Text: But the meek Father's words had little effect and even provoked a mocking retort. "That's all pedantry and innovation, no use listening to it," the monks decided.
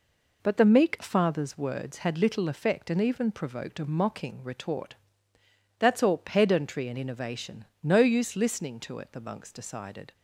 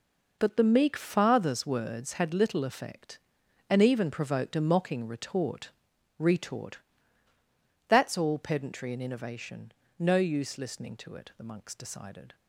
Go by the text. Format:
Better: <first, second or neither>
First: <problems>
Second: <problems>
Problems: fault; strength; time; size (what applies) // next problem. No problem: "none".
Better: first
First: none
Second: says "retort" twice; at 6.1 s